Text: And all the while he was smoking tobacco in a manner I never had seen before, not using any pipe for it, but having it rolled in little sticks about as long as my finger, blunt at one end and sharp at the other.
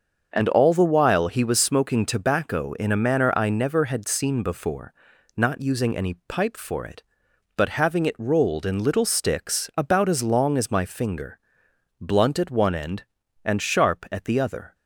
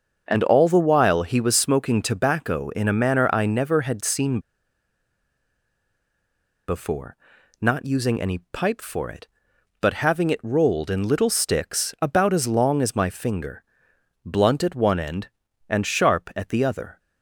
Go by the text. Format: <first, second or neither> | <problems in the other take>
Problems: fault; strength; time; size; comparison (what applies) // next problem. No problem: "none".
first | starts louder than the rest; until 1.2 s; 6.5 dB; also in the first // pauses between "seen" and "before"; strong; at 4.4 s; 2.2 s long